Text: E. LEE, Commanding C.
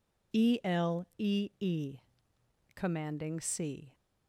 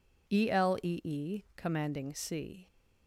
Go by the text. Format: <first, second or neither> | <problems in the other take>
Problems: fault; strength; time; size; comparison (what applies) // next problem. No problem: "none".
neither | none